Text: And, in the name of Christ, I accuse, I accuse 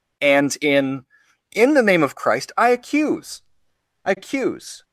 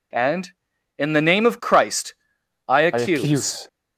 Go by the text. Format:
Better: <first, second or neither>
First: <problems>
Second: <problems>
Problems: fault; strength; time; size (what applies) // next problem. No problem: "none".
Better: second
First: says "in" twice; at 1.5 s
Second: none